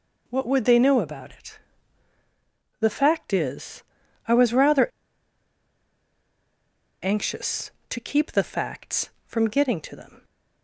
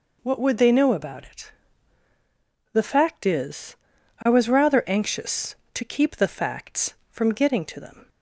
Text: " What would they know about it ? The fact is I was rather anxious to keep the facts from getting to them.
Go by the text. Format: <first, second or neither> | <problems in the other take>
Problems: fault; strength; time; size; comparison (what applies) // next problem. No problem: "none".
second | pauses between "is" and "I"; at 3.8 s; 0.44 s long; also in the second // pauses between "rather" and "anxious"; strong; at 4.8 s; 2.1 s long